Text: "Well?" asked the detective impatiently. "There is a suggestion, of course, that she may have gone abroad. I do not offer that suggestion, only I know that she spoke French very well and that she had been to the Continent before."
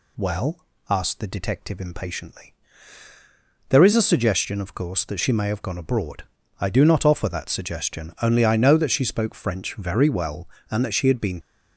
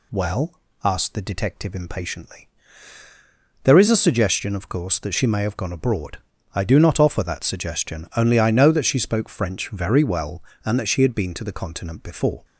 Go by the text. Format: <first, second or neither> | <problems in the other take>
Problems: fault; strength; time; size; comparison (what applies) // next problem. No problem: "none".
second | stops before "to the Continent before"; at 11.4 s